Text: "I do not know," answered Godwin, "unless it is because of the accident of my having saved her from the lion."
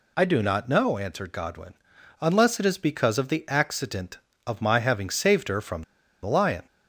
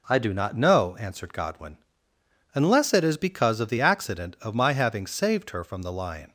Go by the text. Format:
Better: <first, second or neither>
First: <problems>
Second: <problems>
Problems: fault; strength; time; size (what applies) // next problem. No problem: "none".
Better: second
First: pauses between "from" and "the"; at 5.8 s; 0.40 s long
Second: none